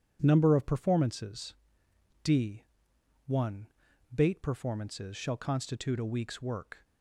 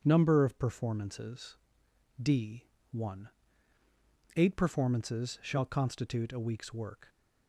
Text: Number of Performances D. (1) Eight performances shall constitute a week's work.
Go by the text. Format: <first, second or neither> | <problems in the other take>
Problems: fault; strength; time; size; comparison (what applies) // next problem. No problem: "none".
second | pauses between "Performances" and "D"; noticeable; at 1.5 s; 0.68 s long; noticeable in the second // says "Bait" for "Eight"; at 4.1 s